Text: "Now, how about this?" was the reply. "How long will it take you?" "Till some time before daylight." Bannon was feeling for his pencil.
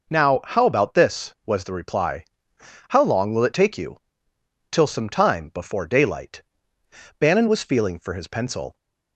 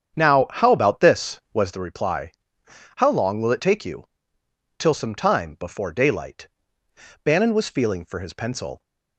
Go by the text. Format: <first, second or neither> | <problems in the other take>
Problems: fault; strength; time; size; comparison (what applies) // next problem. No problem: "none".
first | starts louder than the rest; strong; until 1.9 s; 8 dB